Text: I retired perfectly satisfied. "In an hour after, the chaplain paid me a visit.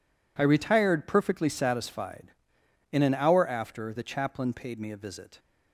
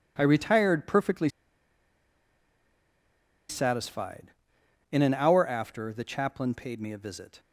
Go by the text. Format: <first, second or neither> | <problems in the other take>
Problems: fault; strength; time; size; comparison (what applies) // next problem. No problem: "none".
first | pauses between "perfectly" and "satisfied"; strong; at 1.2 s; 2.2 s long